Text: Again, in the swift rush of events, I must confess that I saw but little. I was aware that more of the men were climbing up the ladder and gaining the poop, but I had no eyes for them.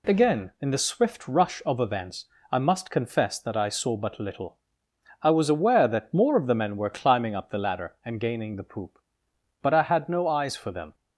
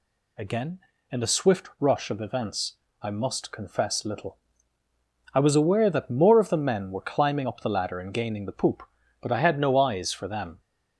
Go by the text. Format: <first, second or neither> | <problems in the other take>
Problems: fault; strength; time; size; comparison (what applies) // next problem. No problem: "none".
first | skips "that I saw but"; at 4.0 s